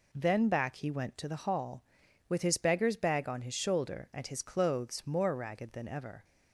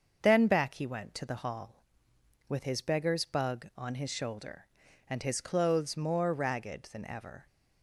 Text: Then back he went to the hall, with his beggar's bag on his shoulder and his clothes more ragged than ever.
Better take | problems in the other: first | starts louder than the rest; until 1.2 s; 6.5 dB // says "bug" for "bag"; at 3.2 s

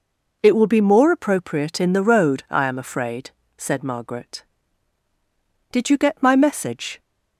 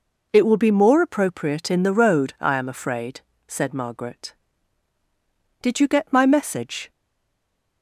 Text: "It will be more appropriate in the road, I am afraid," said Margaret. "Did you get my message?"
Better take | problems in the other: first | stays silent after the last word; slight; from 6.9 s on; 0.9 s long

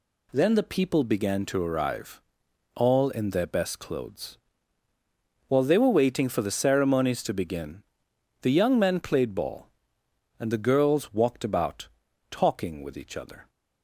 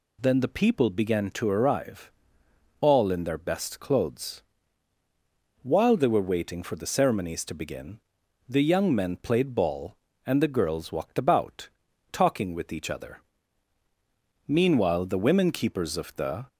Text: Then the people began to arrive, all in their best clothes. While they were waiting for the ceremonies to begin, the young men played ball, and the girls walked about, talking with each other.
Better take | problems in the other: first | goes on to say "Meanwhile the women Keepers of the"; strong; from 14.4 s on; 2.0 s long

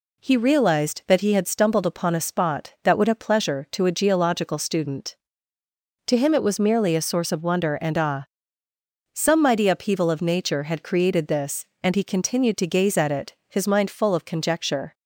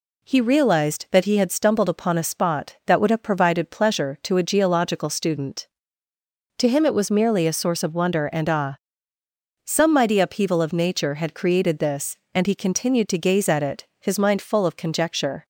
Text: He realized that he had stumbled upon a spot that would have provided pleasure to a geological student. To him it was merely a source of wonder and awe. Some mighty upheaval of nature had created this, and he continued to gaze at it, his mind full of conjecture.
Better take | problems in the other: second | skips "provided"; at 3.1 s

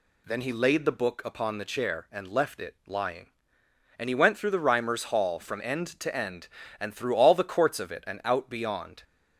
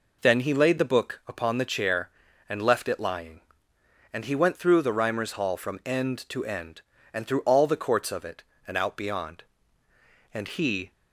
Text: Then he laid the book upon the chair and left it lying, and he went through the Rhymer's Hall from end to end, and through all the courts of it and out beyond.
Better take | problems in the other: first | goes on to say "And he"; from 10.3 s on; 0.58 s long

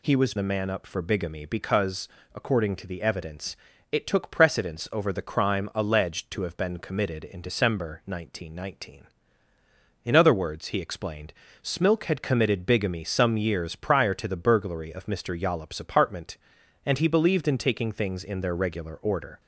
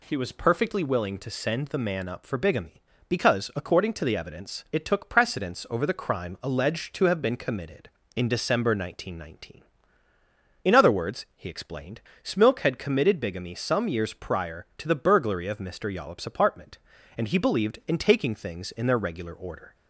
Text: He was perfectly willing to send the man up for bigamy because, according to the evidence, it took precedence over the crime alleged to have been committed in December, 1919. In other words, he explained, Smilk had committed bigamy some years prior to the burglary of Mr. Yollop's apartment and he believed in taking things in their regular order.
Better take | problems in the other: second | skips "perfectly willing to send"; at 0.3 s

